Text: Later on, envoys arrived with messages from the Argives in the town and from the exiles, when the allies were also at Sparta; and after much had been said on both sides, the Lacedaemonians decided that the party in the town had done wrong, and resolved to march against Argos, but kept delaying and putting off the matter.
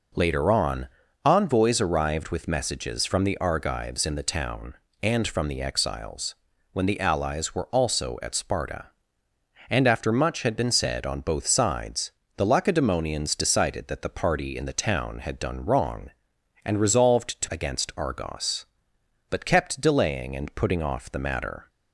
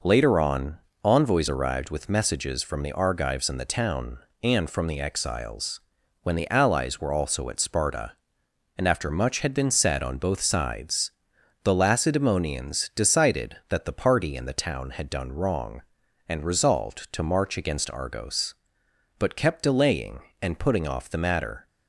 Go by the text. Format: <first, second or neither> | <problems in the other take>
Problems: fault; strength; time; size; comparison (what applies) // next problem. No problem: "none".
second | skips "march"; at 17.4 s